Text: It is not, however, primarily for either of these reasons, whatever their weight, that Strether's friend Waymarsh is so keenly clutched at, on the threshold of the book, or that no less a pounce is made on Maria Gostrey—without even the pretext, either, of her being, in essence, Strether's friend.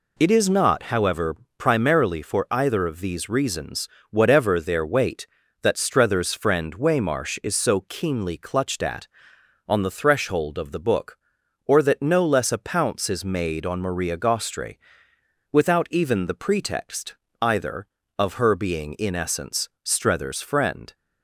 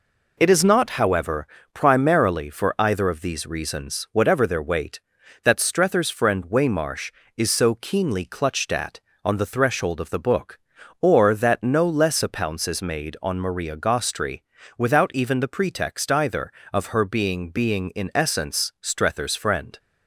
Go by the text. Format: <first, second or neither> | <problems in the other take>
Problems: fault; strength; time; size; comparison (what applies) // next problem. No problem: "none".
first | says "being" twice; at 17.5 s